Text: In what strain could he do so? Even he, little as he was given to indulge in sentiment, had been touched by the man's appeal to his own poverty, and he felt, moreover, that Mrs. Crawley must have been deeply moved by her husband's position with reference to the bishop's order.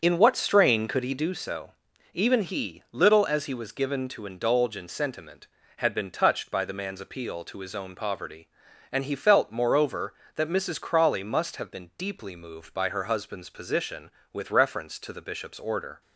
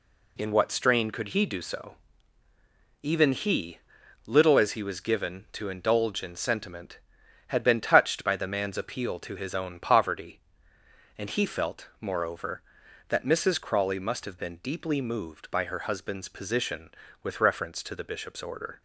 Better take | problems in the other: second | starts louder than the rest; until 1.4 s; 6.5 dB

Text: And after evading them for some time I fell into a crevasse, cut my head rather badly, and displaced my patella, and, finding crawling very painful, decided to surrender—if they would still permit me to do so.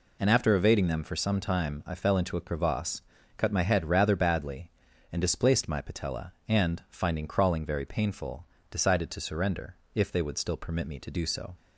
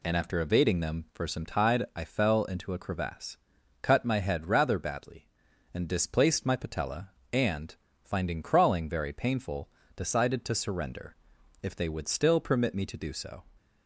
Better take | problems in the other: first | says "tide" for "time"; at 1.4 s

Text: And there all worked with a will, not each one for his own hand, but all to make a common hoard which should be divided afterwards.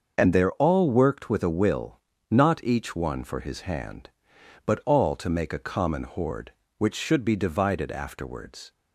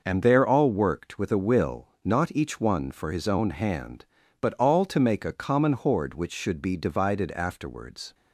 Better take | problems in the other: second | starts louder than the rest; until 1.1 s; 6.5 dB // skips "own"; at 3.6 s

